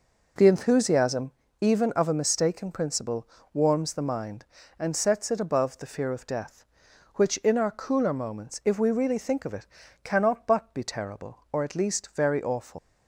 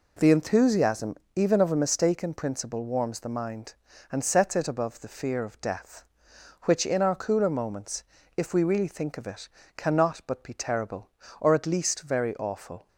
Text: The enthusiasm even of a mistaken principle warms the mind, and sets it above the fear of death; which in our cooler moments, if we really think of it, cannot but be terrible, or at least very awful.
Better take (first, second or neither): second